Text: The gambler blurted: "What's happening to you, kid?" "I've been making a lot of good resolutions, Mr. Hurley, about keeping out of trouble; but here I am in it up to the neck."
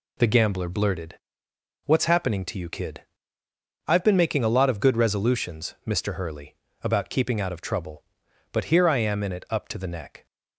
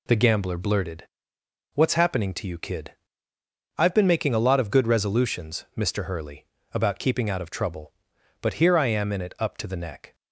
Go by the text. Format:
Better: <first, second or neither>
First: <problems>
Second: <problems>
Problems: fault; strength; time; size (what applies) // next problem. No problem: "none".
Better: neither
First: none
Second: none